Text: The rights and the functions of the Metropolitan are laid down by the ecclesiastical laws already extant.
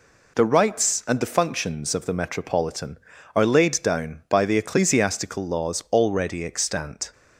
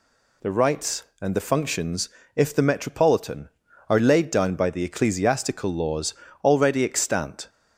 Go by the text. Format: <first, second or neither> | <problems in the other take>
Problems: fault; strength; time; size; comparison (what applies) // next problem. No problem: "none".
first | says "if" for "of"; at 2.3 s // pauses between "laws" and "already"; slight; at 6.1 s; 0.28 s long